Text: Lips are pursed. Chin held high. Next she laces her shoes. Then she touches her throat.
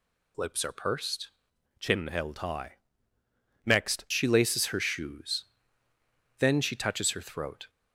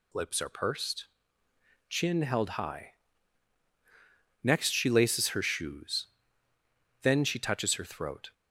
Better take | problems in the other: second | changes voice from "Chin" to "Next"; from 1.7 to 4.0 s; 2.3 s long

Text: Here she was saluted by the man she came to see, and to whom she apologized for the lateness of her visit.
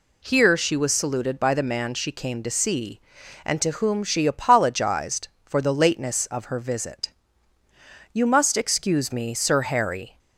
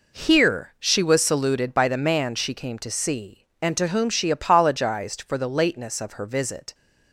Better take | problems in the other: second | goes on to say "You must excuse me Sir Harry"; strong; from 8.1 s on; 2.0 s long

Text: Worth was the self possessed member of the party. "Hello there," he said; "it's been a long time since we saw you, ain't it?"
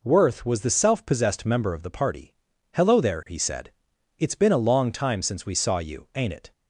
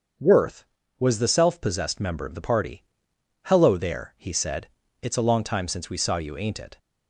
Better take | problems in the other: first | starts louder than the rest; until 1.5 s; 6.5 dB // skips "been"; at 5.1 s

